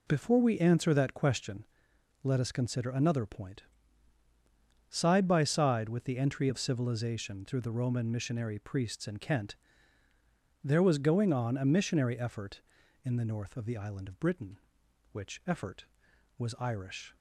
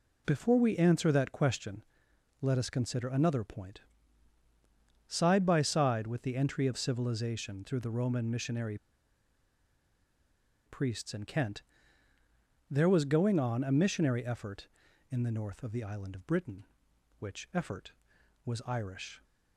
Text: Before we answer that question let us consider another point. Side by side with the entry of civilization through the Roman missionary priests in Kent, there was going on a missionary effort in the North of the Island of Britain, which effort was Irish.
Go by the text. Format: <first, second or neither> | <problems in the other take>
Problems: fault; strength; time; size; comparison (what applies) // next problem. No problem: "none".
first | pauses between "question" and "let"; noticeable; at 1.8 s; 0.58 s long; noticeable in the first // pauses between "missionary" and "priests"; strong; at 8.7 s; 1.9 s long